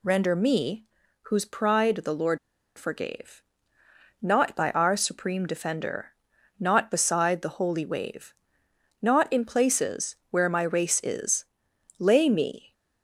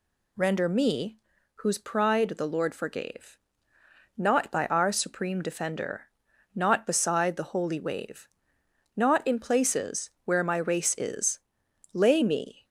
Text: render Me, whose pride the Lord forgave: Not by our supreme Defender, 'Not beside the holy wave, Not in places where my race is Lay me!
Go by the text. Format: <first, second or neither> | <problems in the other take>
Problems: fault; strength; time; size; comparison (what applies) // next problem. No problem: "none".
second | pauses between "Lord" and "forgave"; at 2.3 s; 0.40 s long // pauses between "places" and "where"; slight; at 10.1 s; 0.16 s long; slight in the second // pauses between "is" and "Lay"; noticeable; at 11.4 s; 0.56 s long; noticeable in the second